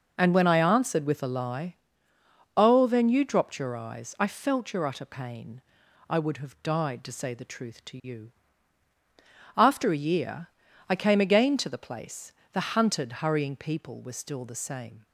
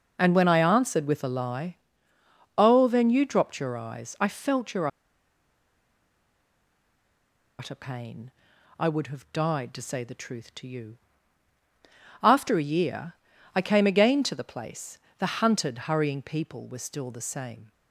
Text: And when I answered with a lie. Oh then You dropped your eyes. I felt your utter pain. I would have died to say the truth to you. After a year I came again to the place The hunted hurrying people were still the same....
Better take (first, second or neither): first